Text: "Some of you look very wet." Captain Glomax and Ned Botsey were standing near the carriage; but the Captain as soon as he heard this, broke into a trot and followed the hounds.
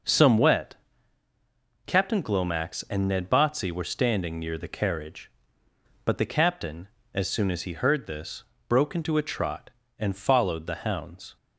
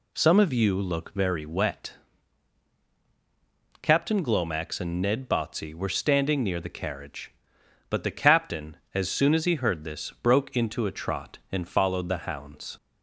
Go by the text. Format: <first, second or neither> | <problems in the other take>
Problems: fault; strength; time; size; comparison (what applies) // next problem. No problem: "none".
second | skips "of you look very"; at 0.3 s